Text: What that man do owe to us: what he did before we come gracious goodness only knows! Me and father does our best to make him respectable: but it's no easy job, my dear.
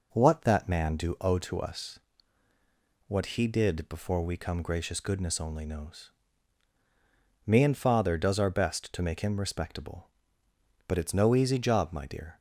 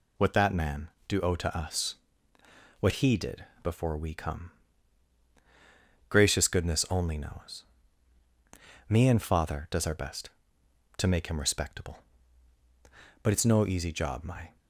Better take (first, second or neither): first